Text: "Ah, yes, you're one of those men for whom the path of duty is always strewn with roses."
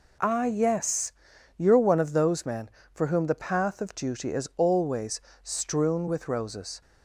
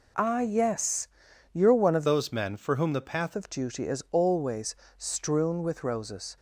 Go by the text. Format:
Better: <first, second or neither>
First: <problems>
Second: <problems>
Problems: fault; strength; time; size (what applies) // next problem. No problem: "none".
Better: first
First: pauses between "always" and "strewn"; slight; at 5.2 s; 0.22 s long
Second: changes voice from "those" to "path"; from 2.0 to 3.3 s; 1.3 s long // pauses between "always" and "strewn"; slight; at 4.7 s; 0.22 s long